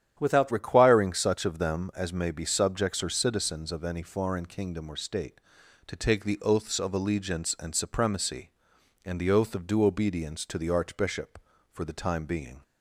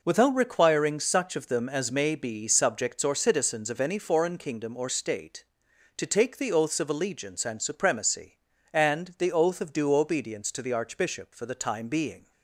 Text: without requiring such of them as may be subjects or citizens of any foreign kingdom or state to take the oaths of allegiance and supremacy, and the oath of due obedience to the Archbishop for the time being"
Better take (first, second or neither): second